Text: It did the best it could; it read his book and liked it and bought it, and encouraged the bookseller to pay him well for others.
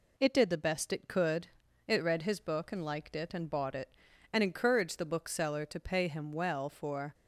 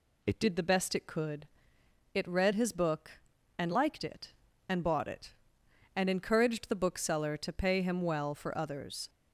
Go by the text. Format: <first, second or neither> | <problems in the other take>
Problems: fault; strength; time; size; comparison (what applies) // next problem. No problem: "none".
second | stops before "others"; at 7.1 s